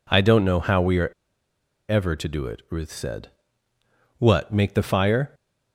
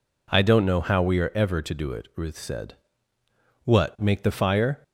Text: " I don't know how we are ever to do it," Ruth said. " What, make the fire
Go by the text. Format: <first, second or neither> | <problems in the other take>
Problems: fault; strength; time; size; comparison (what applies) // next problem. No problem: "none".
second | pauses between "are" and "ever"; noticeable; at 1.0 s; 0.78 s long